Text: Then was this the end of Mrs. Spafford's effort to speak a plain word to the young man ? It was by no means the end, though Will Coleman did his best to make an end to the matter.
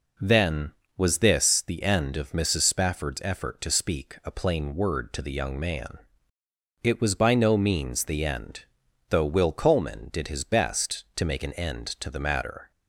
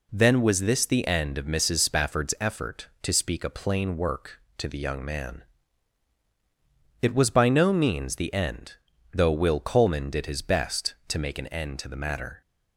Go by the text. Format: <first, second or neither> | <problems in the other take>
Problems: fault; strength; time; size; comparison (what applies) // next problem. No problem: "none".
first | says "work" for "word"; at 3.9 s